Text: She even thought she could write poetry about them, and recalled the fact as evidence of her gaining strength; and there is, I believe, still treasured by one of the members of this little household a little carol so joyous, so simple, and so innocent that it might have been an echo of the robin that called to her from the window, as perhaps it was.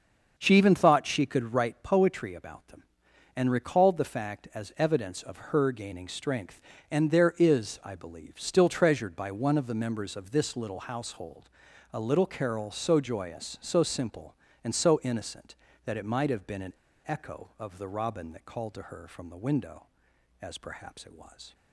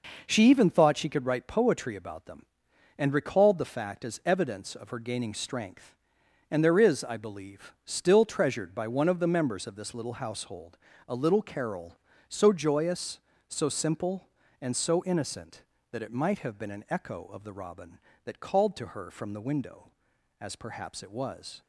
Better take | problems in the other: second | starts louder than the rest; until 1.3 s; 6.5 dB // pauses between "household" and "a"; at 11.4 s; 0.44 s long; slight in the second // pauses between "an" and "echo"; slight; at 16.7 s; 0.34 s long

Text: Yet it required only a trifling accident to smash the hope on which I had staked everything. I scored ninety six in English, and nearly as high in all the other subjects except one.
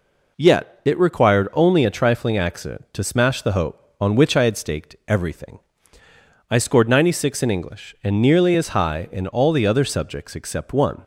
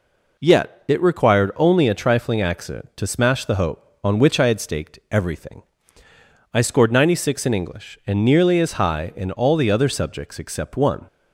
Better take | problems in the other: neither | none

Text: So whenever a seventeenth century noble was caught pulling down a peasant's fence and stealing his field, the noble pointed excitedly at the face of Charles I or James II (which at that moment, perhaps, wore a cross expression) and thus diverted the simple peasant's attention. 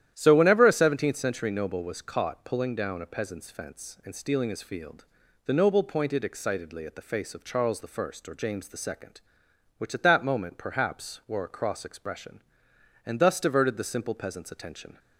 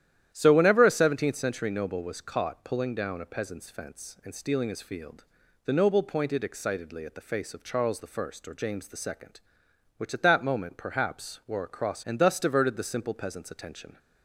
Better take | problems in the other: first | starts louder than the rest; strong; until 1.3 s; 11 dB; strong in the first // skips "expression"; at 12.0 s

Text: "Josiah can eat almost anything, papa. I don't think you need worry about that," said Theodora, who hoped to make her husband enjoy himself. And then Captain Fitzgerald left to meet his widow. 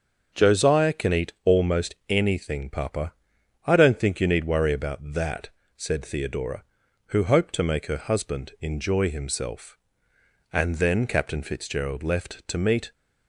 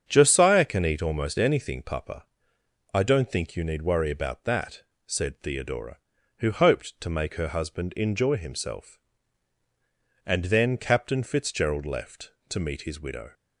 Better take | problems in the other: second | starts louder than the rest; until 1.4 s; 6.5 dB; strong in the second // stops before "his widow"; at 12.9 s

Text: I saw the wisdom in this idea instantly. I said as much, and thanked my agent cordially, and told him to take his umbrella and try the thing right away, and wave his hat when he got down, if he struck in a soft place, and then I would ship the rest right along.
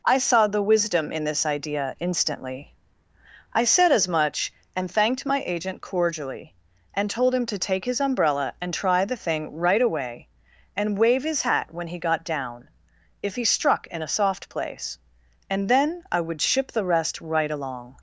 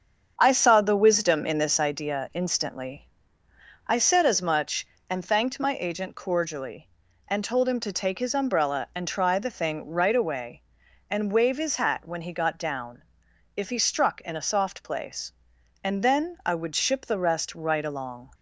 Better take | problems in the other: first | starts louder than the rest; strong; until 2.1 s; 7.5 dB

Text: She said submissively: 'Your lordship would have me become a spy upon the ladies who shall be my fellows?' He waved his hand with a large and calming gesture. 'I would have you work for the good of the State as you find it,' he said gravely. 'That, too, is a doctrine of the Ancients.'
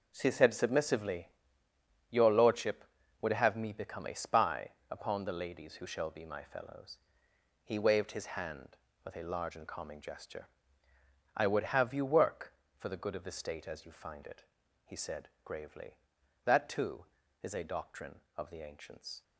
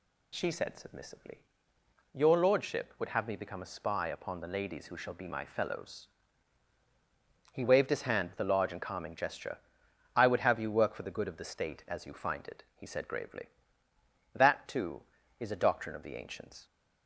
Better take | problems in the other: second | gets quieter; strong; throughout; 10.5 dB // pauses between "spy" and "upon"; slight; at 4.7 s; 0.18 s long // pauses between "said" and "gravely"; slight; at 15.2 s; 0.16 s long

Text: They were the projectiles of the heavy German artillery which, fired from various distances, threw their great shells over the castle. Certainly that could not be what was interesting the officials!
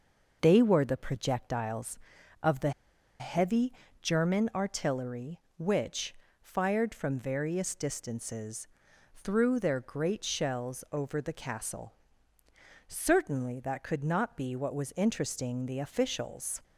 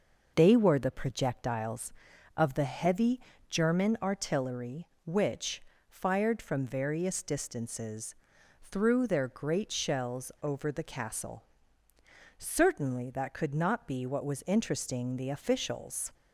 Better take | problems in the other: second | pauses between "the" and "heavy"; noticeable; at 2.7 s; 0.49 s long // pauses between "heavy" and "German"; slight; at 3.7 s; 0.28 s long; slight in the second

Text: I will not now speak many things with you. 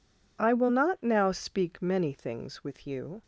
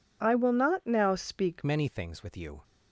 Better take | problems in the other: first | changes voice at "many"; from 1.6 s on; 1.0 s long

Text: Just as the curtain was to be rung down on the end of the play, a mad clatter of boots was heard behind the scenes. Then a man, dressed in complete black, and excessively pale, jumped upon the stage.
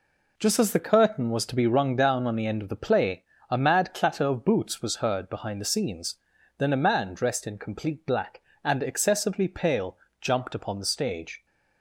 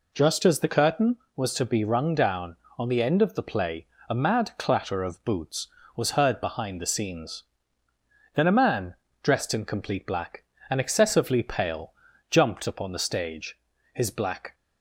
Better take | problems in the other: first | goes on to say "His black"; from 13.9 s on; 0.60 s long

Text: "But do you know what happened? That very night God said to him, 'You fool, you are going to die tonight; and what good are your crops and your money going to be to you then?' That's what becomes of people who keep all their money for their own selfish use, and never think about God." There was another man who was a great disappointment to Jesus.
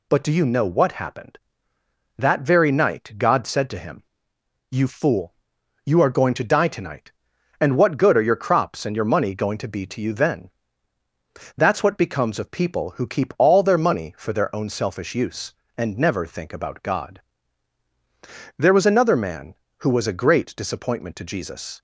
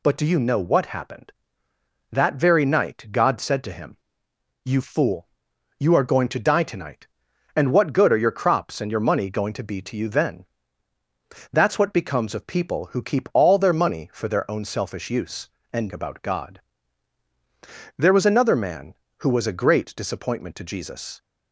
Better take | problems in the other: first | skips "never think"; at 15.9 s

